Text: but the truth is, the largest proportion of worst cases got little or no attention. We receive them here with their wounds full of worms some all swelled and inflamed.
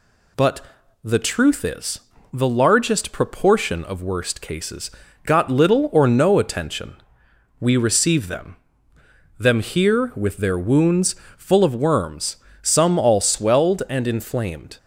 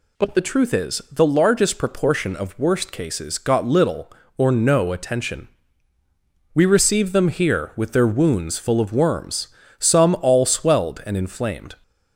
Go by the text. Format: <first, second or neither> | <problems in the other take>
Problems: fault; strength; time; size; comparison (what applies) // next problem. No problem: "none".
second | pauses between "but" and "the"; at 0.6 s; 0.42 s long // pauses between "cases" and "got"; slight; at 4.9 s; 0.34 s long // says "them" twice; at 9.3 s // pauses between "wounds" and "full"; slight; at 11.1 s; 0.24 s long // pauses between "worms" and "some"; slight; at 12.3 s; 0.24 s long; slight in the second